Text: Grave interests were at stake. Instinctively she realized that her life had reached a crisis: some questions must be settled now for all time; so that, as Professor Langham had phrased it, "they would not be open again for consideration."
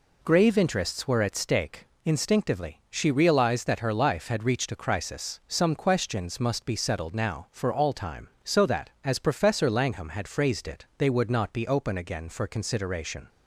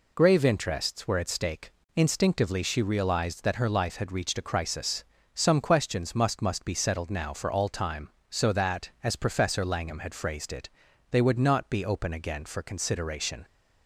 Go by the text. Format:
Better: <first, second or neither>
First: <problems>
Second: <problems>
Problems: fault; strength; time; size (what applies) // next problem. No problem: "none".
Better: first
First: none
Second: says "must" twice; at 6.4 s